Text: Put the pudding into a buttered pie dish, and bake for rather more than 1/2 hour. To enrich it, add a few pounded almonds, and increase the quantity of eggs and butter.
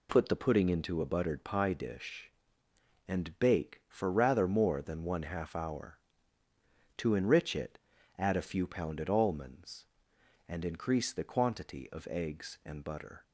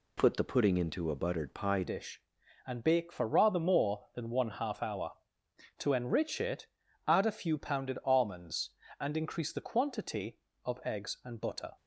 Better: first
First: none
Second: changes voice at "dish"; from 1.8 s on; 9.9 s long

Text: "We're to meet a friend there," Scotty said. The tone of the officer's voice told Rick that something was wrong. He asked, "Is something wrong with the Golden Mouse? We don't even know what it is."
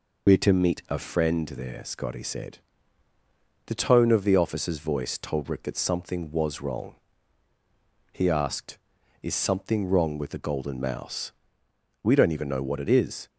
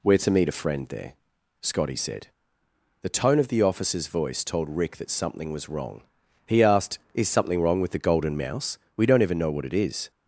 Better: second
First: loses the start of "We're"; at 0.2 s; 60 ms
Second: none

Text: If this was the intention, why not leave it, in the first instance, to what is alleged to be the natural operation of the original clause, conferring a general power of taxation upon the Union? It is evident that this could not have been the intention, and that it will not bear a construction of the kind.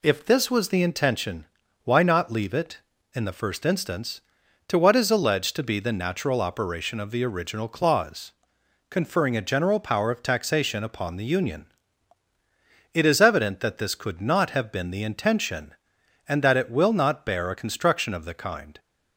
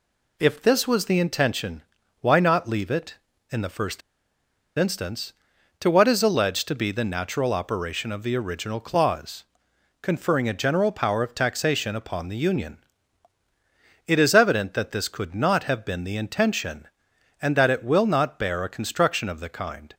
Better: first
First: none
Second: pauses between "first" and "instance"; noticeable; at 4.0 s; 0.77 s long

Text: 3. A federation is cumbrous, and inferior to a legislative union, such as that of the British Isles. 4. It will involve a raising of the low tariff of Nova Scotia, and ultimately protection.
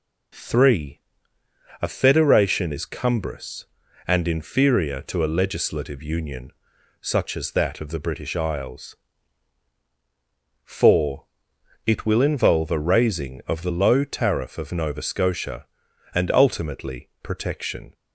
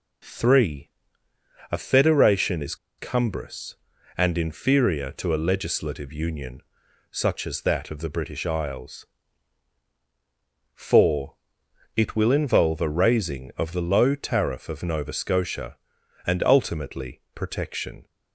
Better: first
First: none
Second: pauses between "is" and "cumbrous"; slight; at 2.7 s; 0.23 s long

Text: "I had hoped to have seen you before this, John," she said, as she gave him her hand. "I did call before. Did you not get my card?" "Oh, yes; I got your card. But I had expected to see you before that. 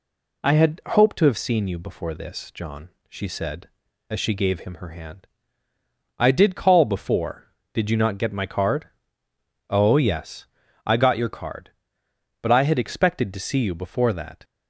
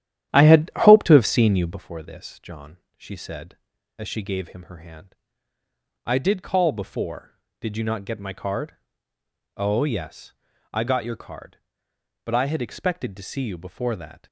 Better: first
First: none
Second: starts louder than the rest; strong; until 1.8 s; 11.5 dB

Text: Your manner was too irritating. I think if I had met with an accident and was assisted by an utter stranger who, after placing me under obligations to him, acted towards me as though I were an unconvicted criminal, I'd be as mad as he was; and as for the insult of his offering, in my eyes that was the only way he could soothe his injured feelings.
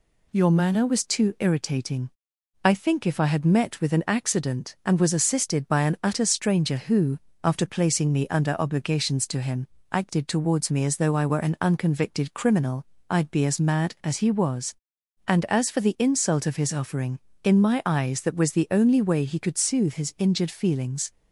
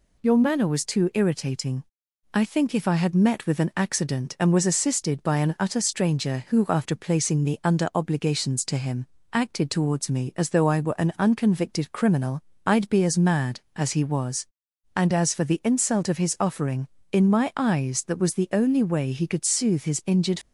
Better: first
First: none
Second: stops before "feelings"; at 20.4 s

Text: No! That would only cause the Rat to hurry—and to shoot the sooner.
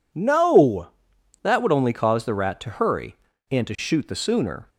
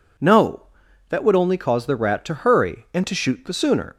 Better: neither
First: none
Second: none

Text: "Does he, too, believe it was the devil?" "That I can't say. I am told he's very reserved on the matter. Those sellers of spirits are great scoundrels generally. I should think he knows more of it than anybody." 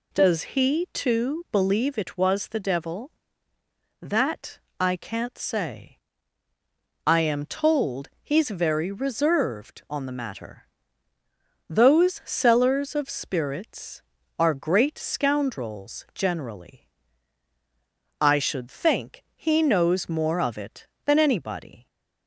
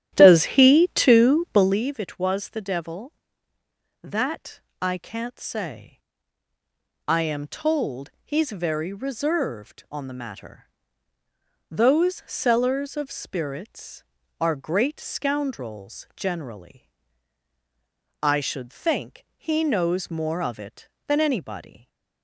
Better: first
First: pauses between "That" and "I"; slight; at 4.5 s; 0.20 s long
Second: starts louder than the rest; strong; until 1.8 s; 12.5 dB // pauses between "That" and "I"; slight; at 4.6 s; 0.20 s long

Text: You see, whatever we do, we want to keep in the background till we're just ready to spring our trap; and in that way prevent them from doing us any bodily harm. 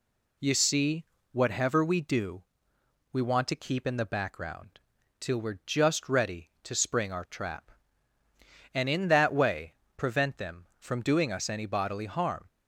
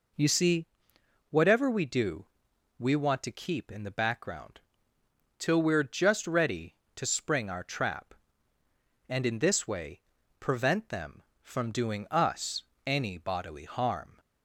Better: first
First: pauses between "background" and "till"; at 4.7 s; 0.40 s long // pauses between "way" and "prevent"; slight; at 9.7 s; 0.24 s long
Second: pauses between "background" and "till"; noticeable; at 4.5 s; 0.80 s long // says "this" for "that"; at 9.3 s // pauses between "way" and "prevent"; at 10.0 s; 0.38 s long // pauses between "us" and "any"; slight; at 12.6 s; 0.22 s long

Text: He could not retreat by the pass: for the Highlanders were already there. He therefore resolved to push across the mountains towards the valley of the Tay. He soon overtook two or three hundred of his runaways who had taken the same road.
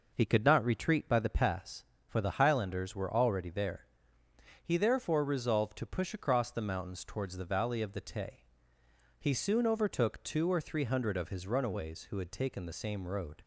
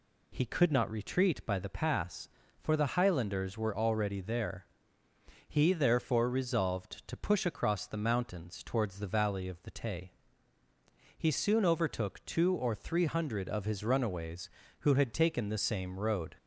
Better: second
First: starts louder than the rest; noticeable; until 1.7 s; 5 dB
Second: none

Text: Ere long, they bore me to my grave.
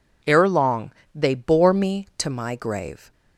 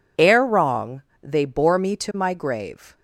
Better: first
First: none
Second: says "wrong" for "long"; at 0.4 s

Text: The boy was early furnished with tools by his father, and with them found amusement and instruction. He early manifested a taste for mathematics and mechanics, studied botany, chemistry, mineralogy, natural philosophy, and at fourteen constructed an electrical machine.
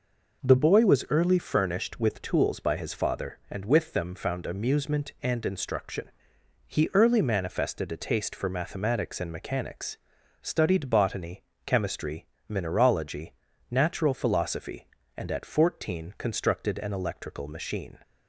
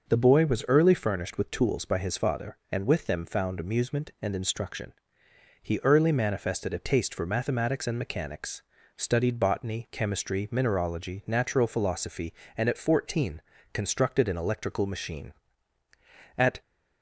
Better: first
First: none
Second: pauses between "fourteen" and "constructed"; slight; at 13.4 s; 0.32 s long // goes on to say "At"; slight; from 16.3 s on; 0.24 s long

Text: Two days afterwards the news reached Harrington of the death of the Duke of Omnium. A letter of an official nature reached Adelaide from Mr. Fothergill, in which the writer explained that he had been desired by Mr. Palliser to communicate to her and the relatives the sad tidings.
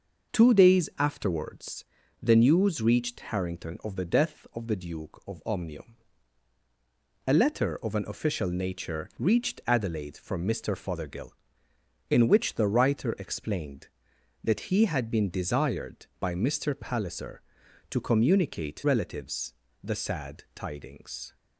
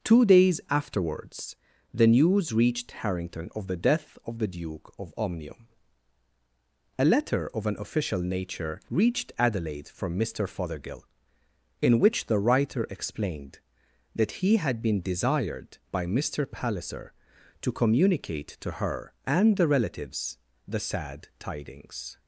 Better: second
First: starts louder than the rest; noticeable; until 1.4 s; 6 dB // pauses between "afterwards" and "the"; slight; at 1.8 s; 0.36 s long // skips "to her and the"; at 18.8 s // pauses between "relatives" and "the"; slight; at 19.5 s; 0.28 s long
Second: starts louder than the rest; noticeable; until 1.1 s; 6 dB // pauses between "afterwards" and "the"; slight; at 1.5 s; 0.36 s long // pauses between "relatives" and "the"; slight; at 20.3 s; 0.28 s long

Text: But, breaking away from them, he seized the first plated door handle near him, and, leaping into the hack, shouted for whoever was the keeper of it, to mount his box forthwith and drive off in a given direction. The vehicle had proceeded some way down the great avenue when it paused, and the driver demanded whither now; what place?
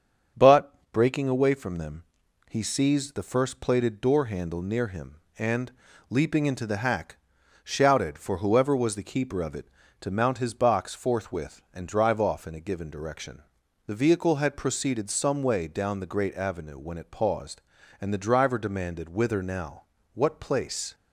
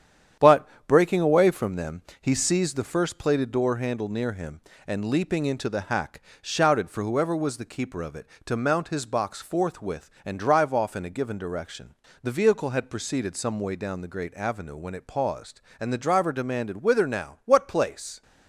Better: first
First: starts louder than the rest; strong; until 1.5 s; 7 dB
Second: gets quieter; noticeable; throughout; 5 dB // starts louder than the rest; strong; until 1.5 s; 9 dB

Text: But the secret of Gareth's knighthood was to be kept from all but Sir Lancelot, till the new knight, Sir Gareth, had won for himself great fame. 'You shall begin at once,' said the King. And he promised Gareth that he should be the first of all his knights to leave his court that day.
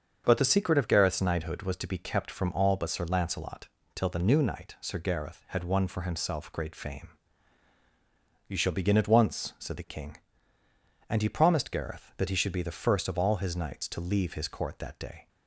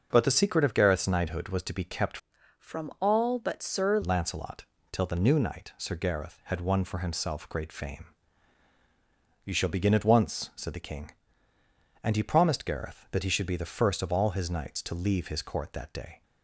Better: first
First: starts louder than the rest; until 1.2 s; 7 dB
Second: starts louder than the rest; noticeable; until 1.1 s; 6 dB // changes voice from "from" to "Sir"; from 2.5 to 3.9 s; 1.4 s long

